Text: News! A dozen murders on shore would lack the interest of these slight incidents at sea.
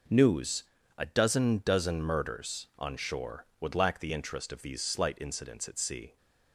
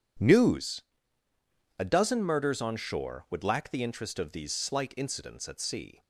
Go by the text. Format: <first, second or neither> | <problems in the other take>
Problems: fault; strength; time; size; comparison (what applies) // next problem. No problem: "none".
second | says "dozen" twice; at 1.6 s